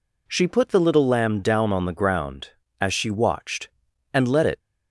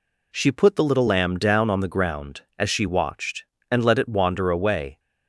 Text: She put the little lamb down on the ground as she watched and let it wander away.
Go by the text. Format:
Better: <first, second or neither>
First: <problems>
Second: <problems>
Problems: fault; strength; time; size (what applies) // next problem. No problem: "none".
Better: second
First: stops before "wander away"; at 4.5 s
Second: none